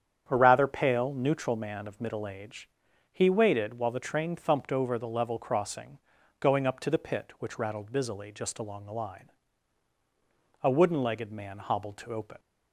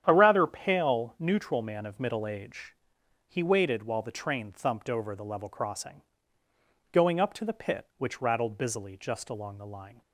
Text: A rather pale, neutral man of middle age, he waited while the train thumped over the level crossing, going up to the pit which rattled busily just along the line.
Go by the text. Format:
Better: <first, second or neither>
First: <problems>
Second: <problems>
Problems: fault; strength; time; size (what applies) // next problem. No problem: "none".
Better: second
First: starts louder than the rest; strong; until 1.2 s; 8.5 dB // goes on to say "A wooden legged man hobbled to open"; strong; from 10.6 s on; 1.7 s long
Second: starts louder than the rest; strong; until 1.0 s; 9.5 dB